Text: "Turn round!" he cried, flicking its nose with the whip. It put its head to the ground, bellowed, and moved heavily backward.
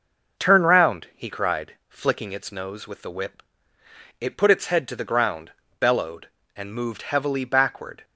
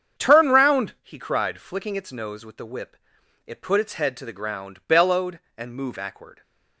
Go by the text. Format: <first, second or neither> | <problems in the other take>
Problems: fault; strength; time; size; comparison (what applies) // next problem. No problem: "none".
first | starts louder than the rest; strong; until 1.2 s; 7.5 dB // skips "heavily"; at 5.9 s